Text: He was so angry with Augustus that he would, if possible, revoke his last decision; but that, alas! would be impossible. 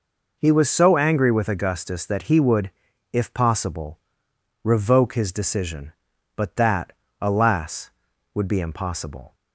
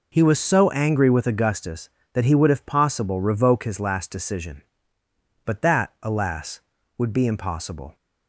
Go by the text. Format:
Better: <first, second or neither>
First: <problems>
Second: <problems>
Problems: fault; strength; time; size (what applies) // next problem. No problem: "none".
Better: second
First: skips "last"; at 5.3 s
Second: none